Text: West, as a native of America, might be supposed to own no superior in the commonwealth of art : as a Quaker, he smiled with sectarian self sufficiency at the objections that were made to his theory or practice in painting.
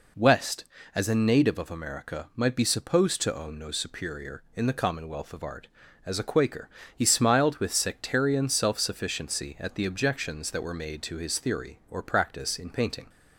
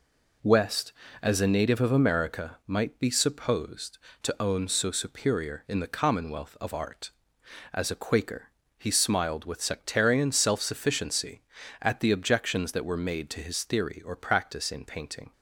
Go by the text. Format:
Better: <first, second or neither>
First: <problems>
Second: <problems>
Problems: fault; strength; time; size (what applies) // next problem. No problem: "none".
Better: first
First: none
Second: says "so" for "no"; at 4.6 s